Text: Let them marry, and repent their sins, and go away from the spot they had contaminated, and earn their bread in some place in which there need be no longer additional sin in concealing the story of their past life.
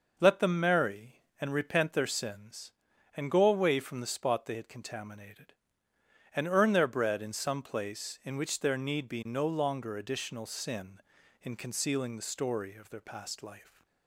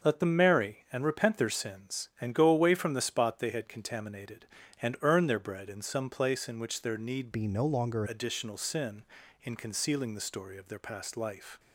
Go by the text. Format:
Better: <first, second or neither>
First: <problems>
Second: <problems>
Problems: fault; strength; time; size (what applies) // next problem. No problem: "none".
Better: first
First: none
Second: starts louder than the rest; until 1.1 s; 6 dB // changes voice from "be" to "longer"; from 7.3 to 8.0 s; 0.7 s long